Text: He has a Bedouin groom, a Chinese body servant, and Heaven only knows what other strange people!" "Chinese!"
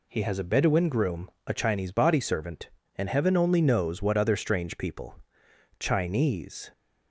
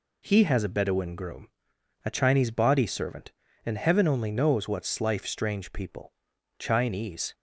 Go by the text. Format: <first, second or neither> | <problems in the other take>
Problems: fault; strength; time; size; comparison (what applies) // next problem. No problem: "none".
first | says "slife" for "other"; at 4.8 s